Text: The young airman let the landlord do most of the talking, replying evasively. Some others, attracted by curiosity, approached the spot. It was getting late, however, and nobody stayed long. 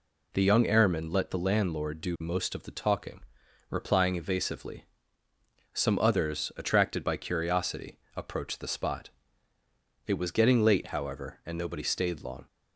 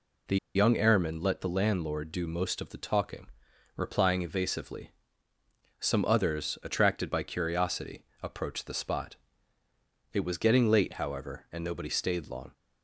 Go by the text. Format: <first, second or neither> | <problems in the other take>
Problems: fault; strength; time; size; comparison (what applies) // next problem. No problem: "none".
first | pauses between "The" and "young"; slight; at 0.3 s; 0.18 s long